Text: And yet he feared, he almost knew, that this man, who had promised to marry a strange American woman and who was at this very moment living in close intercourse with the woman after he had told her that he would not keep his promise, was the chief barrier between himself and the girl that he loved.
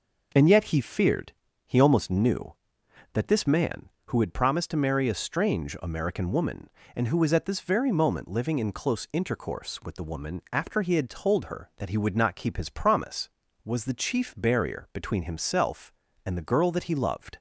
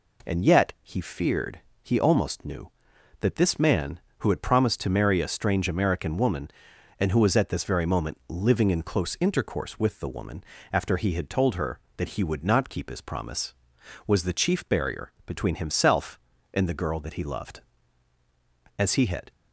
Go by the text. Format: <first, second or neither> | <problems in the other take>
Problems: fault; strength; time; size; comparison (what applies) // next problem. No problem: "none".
first | pauses between "woman" and "after"; slight; at 10.4 s; 0.28 s long // goes on to say "As he had"; from 18.7 s on; 0.54 s long